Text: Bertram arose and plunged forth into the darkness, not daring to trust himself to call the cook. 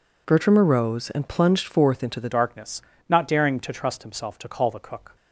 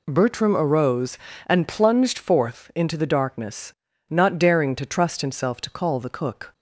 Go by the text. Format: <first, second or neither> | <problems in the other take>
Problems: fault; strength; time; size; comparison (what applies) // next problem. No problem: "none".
second | changes voice at "darkness"; from 2.2 s on; 2.9 s long